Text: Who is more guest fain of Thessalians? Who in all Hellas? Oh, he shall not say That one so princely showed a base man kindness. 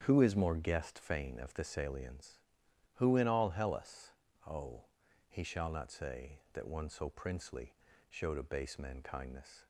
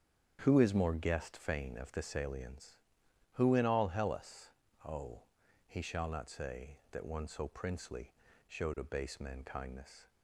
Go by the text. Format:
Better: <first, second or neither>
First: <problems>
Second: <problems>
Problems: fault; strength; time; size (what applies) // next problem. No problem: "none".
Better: neither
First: starts louder than the rest; strong; until 1.0 s; 8.5 dB // pauses between "princely" and "showed"; slight; at 7.7 s; 0.34 s long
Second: starts louder than the rest; strong; until 1.4 s; 8.5 dB // pauses between "princely" and "showed"; slight; at 8.1 s; 0.34 s long